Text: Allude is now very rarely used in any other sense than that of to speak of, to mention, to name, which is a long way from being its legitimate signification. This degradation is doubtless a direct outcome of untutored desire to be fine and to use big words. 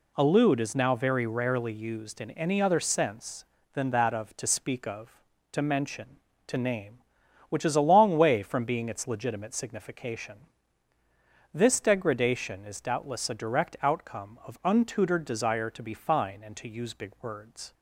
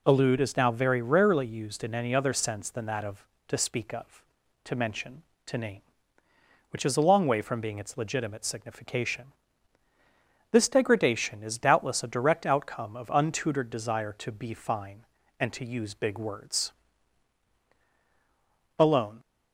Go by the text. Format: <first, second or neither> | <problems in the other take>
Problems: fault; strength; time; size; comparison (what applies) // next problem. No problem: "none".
first | goes on to say "ALONE"; slight; from 18.7 s on; 0.42 s long